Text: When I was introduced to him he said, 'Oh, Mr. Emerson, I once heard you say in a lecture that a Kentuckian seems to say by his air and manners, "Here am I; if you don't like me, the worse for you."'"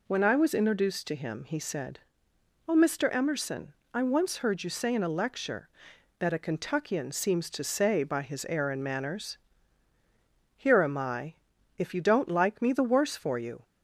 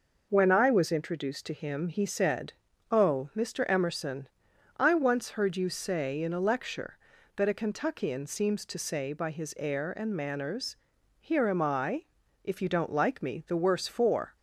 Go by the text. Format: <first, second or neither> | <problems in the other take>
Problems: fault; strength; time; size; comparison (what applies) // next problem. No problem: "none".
first | stops before "you"; at 14.3 s